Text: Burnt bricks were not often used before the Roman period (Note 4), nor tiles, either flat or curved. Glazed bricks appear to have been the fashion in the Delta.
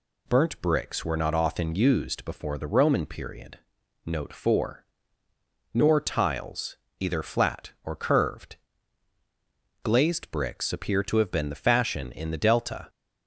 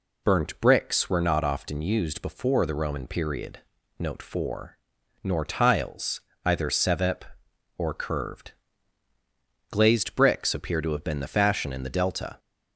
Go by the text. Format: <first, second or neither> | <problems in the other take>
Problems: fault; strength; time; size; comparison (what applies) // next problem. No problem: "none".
first | says "sevep" for "flat"; at 6.7 s